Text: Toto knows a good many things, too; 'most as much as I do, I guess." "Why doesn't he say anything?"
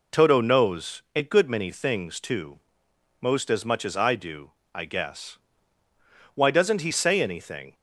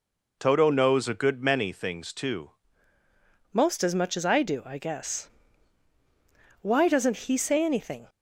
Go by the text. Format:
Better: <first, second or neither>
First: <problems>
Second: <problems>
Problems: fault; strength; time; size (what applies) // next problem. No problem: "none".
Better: first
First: none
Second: changes voice at "most"; from 3.5 s on; 4.5 s long